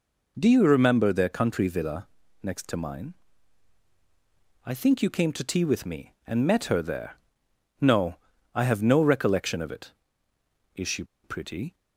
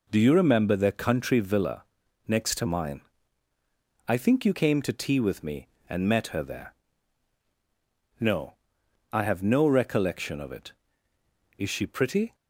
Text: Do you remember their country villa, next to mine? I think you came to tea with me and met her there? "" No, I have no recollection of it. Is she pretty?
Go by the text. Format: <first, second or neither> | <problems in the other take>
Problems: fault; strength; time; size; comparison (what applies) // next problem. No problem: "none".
second | pauses between "she" and "pretty"; slight; at 11.0 s; 0.20 s long